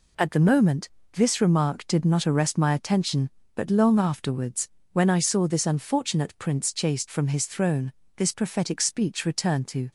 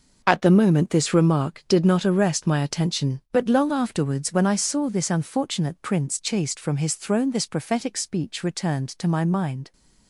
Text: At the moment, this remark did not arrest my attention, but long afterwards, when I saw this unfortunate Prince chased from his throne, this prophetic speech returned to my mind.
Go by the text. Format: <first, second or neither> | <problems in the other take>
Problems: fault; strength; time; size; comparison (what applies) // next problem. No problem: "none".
second | stops before "my mind"; at 9.8 s